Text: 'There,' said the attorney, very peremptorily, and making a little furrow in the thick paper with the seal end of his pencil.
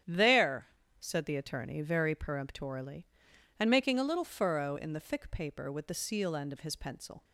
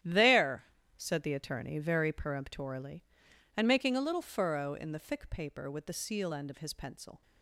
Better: first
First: starts louder than the rest; strong; until 1.3 s; 9.5 dB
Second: gets quieter; strong; throughout; 12 dB // starts louder than the rest; strong; until 1.3 s; 11.5 dB

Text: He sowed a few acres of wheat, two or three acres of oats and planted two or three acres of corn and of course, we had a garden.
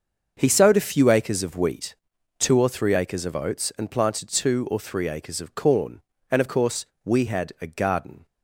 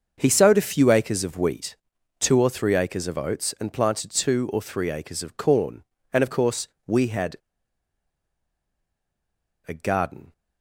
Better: first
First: starts louder than the rest; until 1.3 s; 6.5 dB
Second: starts louder than the rest; until 1.1 s; 6.5 dB // pauses between "had" and "a"; strong; at 7.3 s; 2.3 s long

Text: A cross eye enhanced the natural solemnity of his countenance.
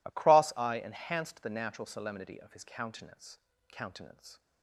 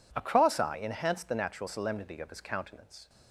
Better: second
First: says "countenance" twice; at 3.7 s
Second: none

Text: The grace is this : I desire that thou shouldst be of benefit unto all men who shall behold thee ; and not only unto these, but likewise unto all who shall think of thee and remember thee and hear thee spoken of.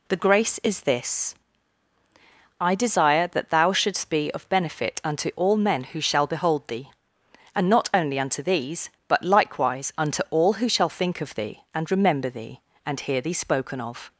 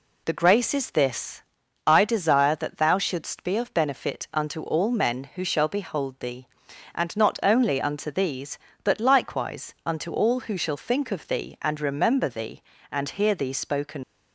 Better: first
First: none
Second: stops before "of"; at 14.0 s

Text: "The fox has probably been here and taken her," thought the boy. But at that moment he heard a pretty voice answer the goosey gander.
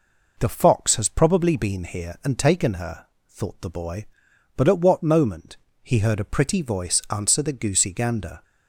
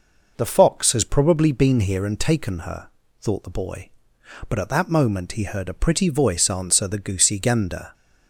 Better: second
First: says "what" for "that"; at 4.7 s // pauses between "moment" and "he"; slight; at 5.5 s; 0.26 s long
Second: none

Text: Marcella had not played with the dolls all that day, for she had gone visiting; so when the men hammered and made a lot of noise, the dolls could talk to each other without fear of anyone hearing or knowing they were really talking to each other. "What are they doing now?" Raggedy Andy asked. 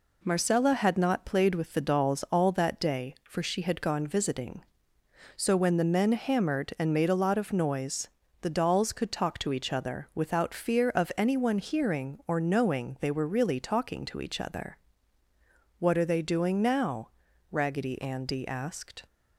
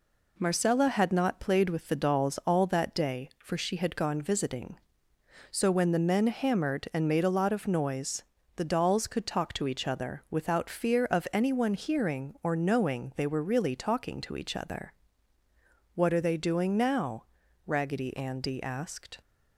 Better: neither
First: none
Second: none

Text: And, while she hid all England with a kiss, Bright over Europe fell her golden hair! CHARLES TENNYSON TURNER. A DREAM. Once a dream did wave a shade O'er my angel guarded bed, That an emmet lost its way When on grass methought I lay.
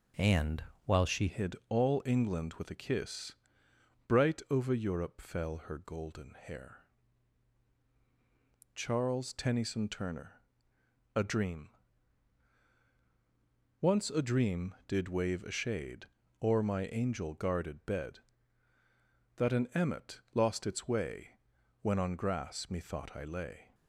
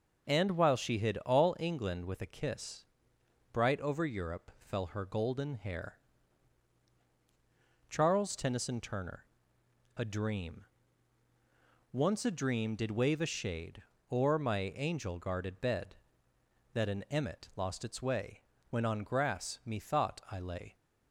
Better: second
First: changes voice at "hid"; from 1.2 s on; 22.5 s long // pauses between "shade" and "O'er"; slight; at 16.0 s; 0.36 s long // pauses between "way" and "When"; noticeable; at 21.3 s; 0.46 s long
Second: pauses between "shade" and "O'er"; slight; at 13.8 s; 0.28 s long // pauses between "way" and "When"; slight; at 18.4 s; 0.28 s long

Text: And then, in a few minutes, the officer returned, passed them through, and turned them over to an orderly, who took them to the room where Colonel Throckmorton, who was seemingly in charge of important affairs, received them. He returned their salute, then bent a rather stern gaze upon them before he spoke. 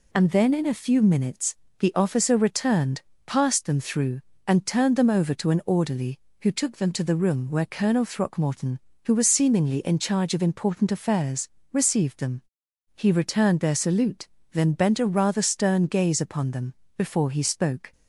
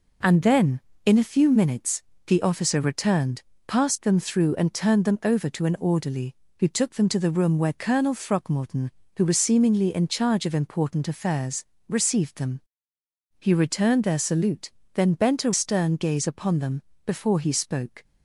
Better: first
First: pauses between "them" and "before"; slight; at 16.7 s; 0.24 s long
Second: skips "rather"; at 15.5 s // pauses between "them" and "before"; slight; at 16.8 s; 0.24 s long

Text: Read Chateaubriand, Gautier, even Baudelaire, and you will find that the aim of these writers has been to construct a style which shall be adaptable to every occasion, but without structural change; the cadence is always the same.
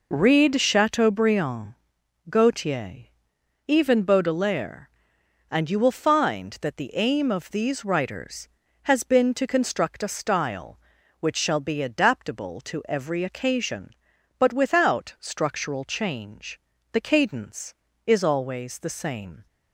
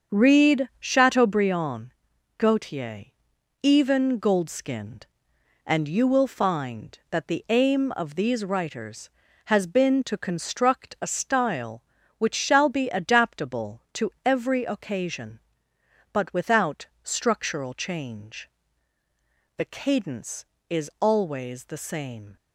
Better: first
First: none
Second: starts louder than the rest; until 1.2 s; 7 dB // says "Goldskinned" for "Baudelaire"; at 4.1 s // pauses between "to" and "every"; slight; at 14.0 s; 0.16 s long // pauses between "without" and "structural"; slight; at 16.8 s; 0.16 s long

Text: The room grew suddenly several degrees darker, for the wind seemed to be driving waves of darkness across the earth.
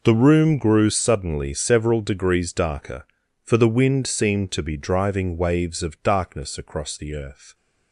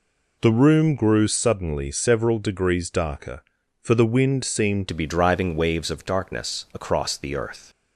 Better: first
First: none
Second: changes voice at "to"; from 4.8 s on; 2.8 s long

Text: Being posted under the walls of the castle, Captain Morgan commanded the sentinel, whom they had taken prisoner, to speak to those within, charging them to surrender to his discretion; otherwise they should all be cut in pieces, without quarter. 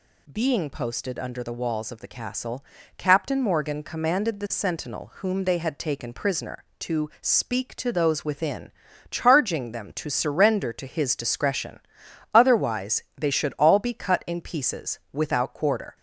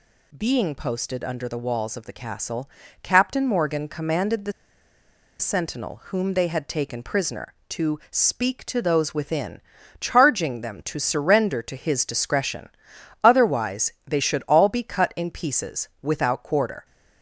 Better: first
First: none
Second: pauses between "the" and "sentinel"; noticeable; at 4.5 s; 0.88 s long

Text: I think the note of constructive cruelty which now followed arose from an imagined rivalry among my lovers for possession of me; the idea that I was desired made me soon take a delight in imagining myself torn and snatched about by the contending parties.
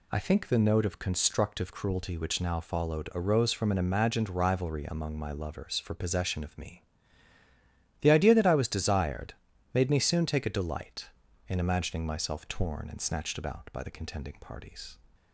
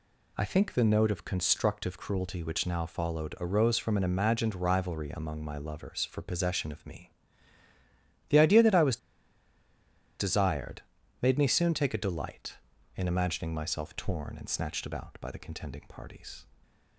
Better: first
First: pauses between "desired" and "made"; at 9.3 s; 0.40 s long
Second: pauses between "was" and "desired"; at 8.9 s; 1.2 s long // pauses between "desired" and "made"; at 10.8 s; 0.40 s long

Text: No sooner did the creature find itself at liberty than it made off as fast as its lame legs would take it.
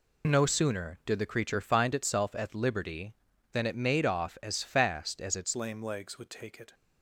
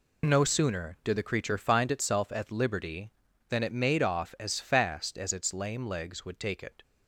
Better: second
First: changes voice at "lame"; from 5.5 s on; 1.2 s long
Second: none

